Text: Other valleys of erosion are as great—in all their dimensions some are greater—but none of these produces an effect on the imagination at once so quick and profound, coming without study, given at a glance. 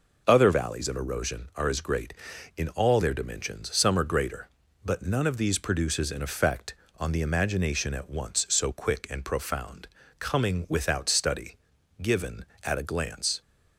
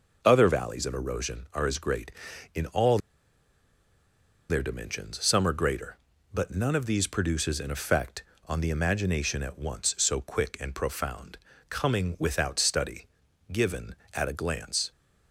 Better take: first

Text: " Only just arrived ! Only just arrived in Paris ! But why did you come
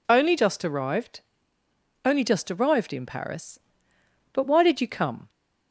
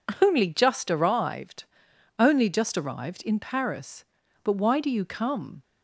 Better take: first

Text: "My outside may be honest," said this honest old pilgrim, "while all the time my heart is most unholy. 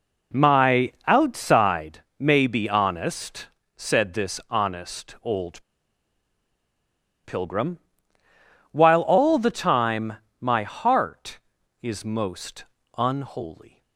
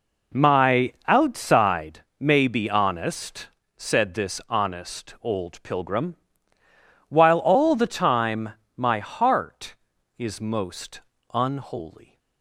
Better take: second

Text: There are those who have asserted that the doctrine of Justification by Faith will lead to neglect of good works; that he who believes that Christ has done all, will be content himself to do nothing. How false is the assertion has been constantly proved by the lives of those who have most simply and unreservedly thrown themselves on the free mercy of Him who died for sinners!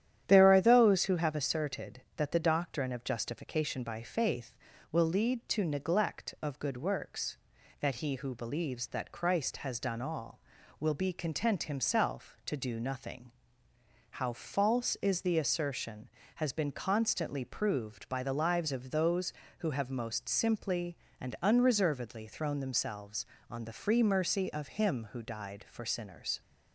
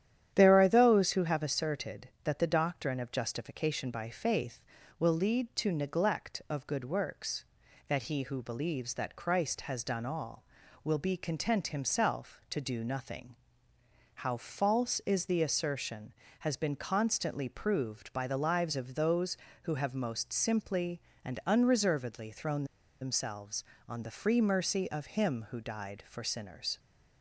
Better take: first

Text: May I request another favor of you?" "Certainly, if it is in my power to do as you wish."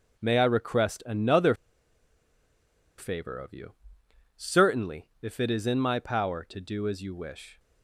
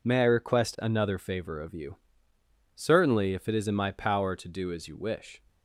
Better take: second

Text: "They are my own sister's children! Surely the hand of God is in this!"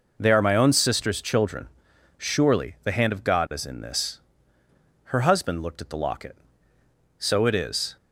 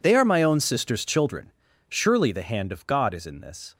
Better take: second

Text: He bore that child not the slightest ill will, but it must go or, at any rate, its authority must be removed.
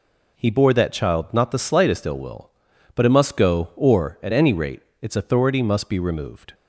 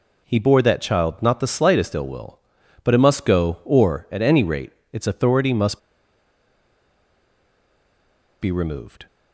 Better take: first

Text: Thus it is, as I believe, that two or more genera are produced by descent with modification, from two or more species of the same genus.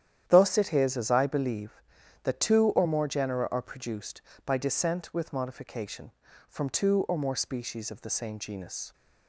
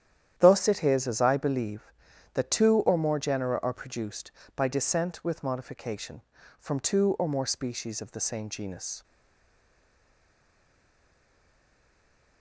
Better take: first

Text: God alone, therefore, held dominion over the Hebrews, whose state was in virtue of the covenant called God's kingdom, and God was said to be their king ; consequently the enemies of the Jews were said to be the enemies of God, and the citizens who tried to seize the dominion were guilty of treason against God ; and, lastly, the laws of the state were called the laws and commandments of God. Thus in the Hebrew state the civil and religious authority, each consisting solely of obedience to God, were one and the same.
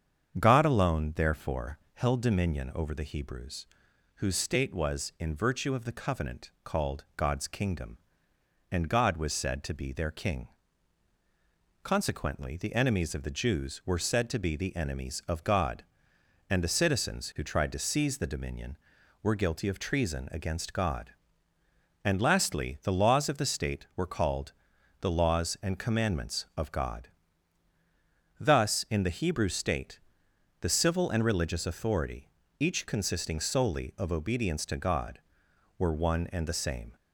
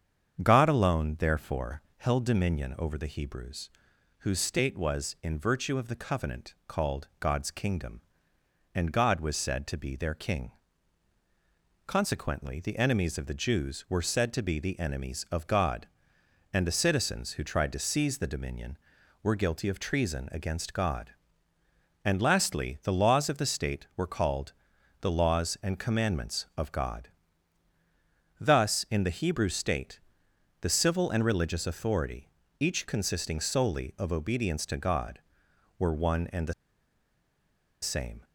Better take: first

